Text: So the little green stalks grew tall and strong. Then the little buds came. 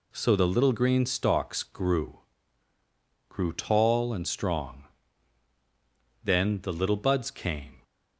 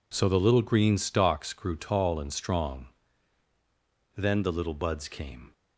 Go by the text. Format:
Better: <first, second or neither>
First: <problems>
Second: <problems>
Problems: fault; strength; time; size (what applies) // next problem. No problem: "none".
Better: second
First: says "grew" twice; at 3.2 s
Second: none